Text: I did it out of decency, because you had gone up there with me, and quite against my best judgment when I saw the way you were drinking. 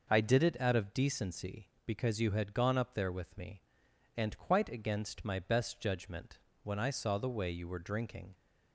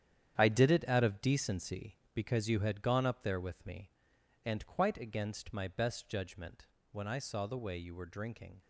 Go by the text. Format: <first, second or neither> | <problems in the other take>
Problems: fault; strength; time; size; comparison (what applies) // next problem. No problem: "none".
first | gets quieter; strong; throughout; 10 dB // pauses between "judgment" and "when"; slight; at 6.6 s; 0.26 s long; slight in the first